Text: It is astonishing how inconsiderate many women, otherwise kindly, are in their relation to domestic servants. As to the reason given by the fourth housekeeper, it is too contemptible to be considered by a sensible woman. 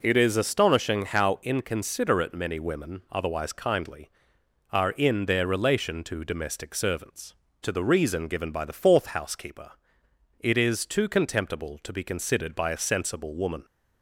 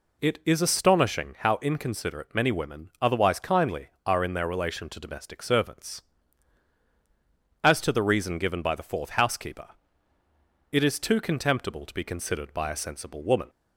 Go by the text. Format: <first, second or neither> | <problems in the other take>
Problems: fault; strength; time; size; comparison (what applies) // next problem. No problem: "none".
second | skips "As"; at 7.4 s